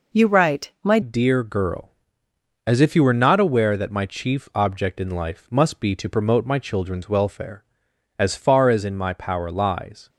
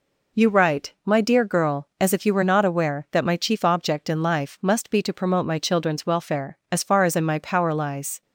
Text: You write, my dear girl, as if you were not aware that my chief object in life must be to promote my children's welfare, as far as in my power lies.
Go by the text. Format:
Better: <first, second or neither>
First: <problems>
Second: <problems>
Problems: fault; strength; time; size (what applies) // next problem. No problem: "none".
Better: second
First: changes voice at "dear"; from 1.0 s on; 9.0 s long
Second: none